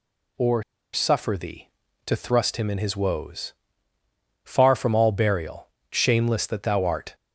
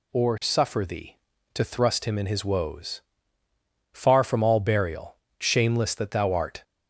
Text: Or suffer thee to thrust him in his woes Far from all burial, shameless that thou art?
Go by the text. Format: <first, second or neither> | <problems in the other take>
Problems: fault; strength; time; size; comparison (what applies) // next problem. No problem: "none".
second | pauses between "Or" and "suffer"; slight; at 0.6 s; 0.30 s long // pauses between "woes" and "Far"; noticeable; at 3.5 s; 0.92 s long; noticeable in the second